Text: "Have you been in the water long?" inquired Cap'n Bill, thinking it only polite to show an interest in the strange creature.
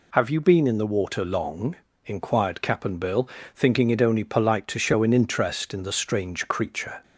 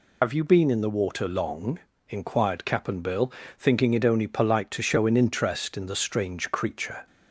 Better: first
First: none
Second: loses the start of "Have"; at 0.2 s; 60 ms

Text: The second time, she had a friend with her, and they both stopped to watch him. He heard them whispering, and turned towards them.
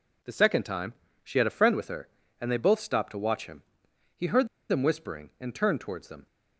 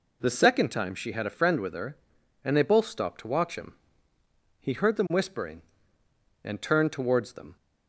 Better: second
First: pauses between "heard" and "them"; slight; at 4.4 s; 0.23 s long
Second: none

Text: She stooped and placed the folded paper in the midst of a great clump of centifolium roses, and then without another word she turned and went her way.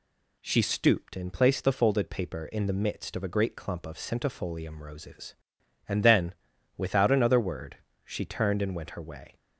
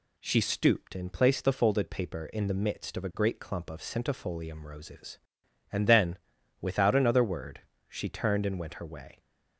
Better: neither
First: pauses between "then" and "without"; at 6.3 s; 0.42 s long // pauses between "word" and "she"; slight; at 7.7 s; 0.28 s long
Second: pauses between "then" and "without"; at 6.1 s; 0.42 s long // pauses between "word" and "she"; slight; at 7.5 s; 0.28 s long

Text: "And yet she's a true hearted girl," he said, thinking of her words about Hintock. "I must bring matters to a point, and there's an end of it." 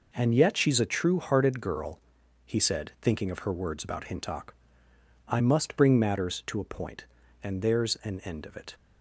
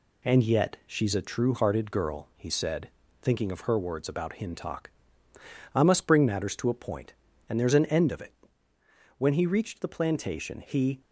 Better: first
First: none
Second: goes on to say "When he reached the plantation he"; strong; from 9.1 s on; 1.8 s long

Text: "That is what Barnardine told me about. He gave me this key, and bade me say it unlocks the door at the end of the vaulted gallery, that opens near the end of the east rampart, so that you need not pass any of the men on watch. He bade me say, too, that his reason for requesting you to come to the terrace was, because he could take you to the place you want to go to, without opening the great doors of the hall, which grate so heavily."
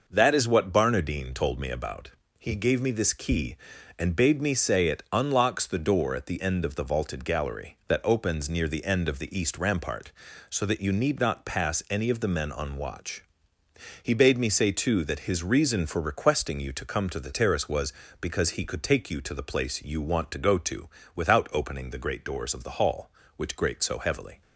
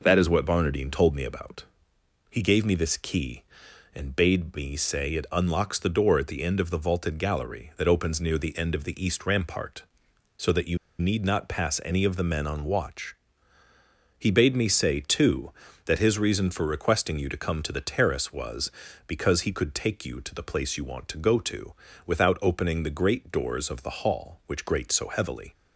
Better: first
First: none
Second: pauses between "you" and "need"; slight; at 10.7 s; 0.21 s long

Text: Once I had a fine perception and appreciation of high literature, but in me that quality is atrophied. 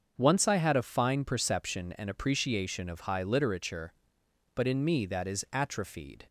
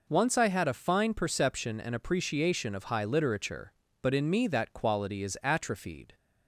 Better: second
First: starts louder than the rest; until 1.1 s; 6.5 dB // skips "quality"; at 5.2 s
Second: none

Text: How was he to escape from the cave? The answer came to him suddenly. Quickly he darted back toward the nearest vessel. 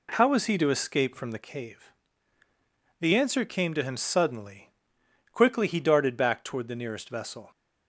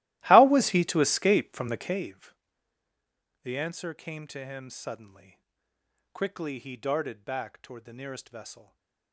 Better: first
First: none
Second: starts louder than the rest; strong; until 2.1 s; 16.5 dB // stays silent after the last word; slight; from 8.6 s on; 0.5 s long

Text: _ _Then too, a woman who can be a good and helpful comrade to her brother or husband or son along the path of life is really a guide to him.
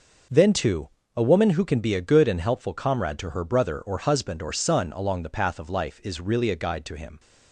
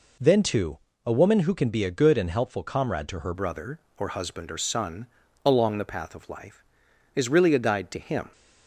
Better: first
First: none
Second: changes voice at "brother"; from 3.3 s on; 5.0 s long // pauses between "son" and "along"; at 5.0 s; 0.38 s long

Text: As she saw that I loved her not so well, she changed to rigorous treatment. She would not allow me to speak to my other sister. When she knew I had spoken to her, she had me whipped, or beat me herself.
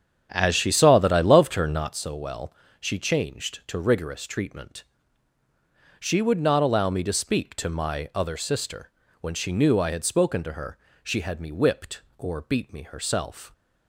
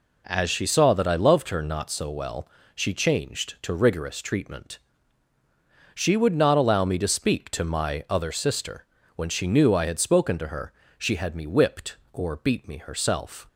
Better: second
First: starts louder than the rest; strong; until 1.9 s; 8.5 dB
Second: none

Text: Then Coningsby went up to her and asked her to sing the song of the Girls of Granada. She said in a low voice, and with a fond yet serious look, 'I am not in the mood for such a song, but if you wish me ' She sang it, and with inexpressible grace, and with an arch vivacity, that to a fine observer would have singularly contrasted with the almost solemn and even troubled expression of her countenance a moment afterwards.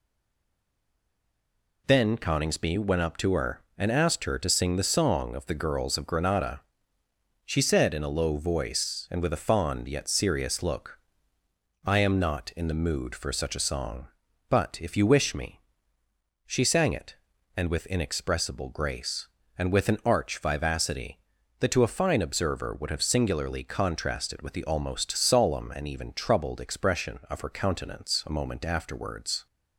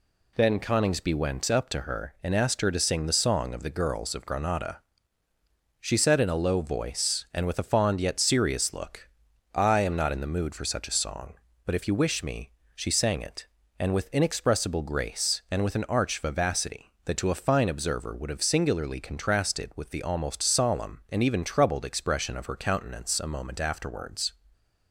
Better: second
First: stays silent before the first word; noticeable; until 1.8 s; 1.8 s long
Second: none

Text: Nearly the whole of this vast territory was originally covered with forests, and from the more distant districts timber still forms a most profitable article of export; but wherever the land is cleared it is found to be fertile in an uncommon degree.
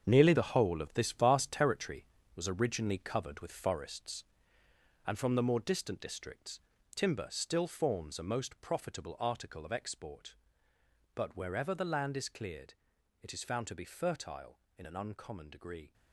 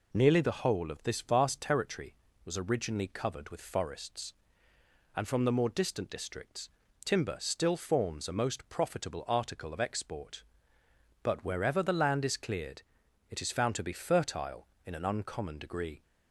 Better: second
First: gets quieter; strong; throughout; 10 dB // pauses between "districts" and "timber"; slight; at 6.5 s; 0.36 s long // pauses between "cleared" and "it"; noticeable; at 12.7 s; 0.48 s long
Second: pauses between "districts" and "timber"; slight; at 6.6 s; 0.36 s long // pauses between "cleared" and "it"; noticeable; at 12.8 s; 0.48 s long

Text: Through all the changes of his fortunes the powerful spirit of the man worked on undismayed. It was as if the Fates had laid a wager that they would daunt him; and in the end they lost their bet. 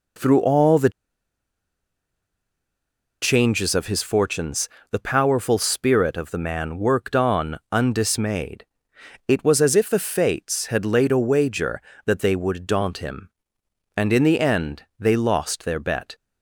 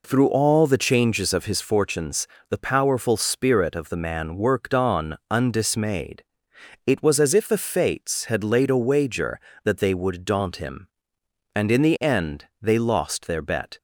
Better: second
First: pauses between "the" and "changes"; strong; at 0.9 s; 2.3 s long // pauses between "fortunes" and "the"; slight; at 4.6 s; 0.22 s long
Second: pauses between "fortunes" and "the"; slight; at 2.2 s; 0.22 s long

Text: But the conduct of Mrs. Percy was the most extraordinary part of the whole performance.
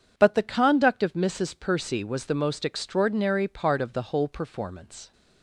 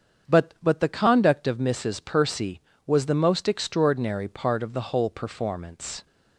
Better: first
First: none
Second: starts louder than the rest; strong; until 1.3 s; 7.5 dB // says "But" twice; at 0.6 s

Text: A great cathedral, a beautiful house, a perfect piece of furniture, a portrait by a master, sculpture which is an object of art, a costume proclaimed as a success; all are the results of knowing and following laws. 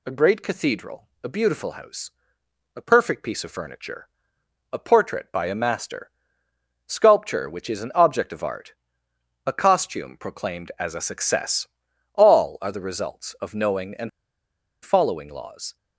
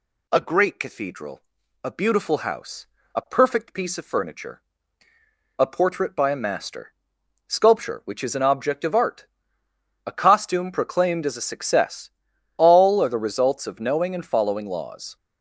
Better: second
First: pauses between "and" and "following"; noticeable; at 14.0 s; 0.74 s long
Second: none

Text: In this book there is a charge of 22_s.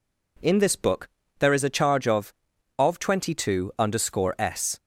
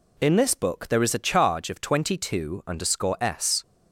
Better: second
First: pauses between "book" and "there"; slight; at 1.0 s; 0.32 s long // says "of" twice; at 2.7 s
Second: none

